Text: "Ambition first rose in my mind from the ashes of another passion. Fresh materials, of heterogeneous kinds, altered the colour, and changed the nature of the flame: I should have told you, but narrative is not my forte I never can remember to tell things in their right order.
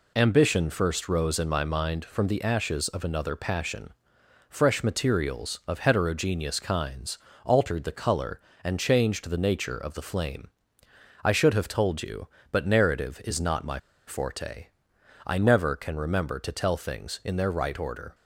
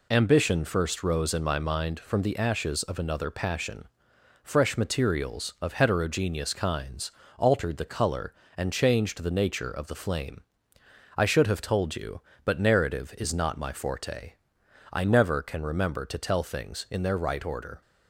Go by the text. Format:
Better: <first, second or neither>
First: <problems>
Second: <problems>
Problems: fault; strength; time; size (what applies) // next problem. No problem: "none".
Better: second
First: pauses between "my" and "forte"; slight; at 13.7 s; 0.27 s long // pauses between "forte" and "I"; noticeable; at 14.6 s; 0.60 s long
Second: pauses between "forte" and "I"; noticeable; at 14.3 s; 0.60 s long